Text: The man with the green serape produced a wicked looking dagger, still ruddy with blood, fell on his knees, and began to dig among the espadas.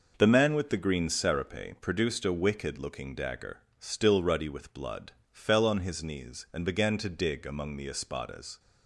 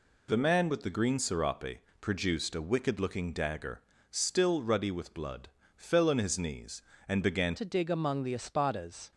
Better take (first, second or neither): first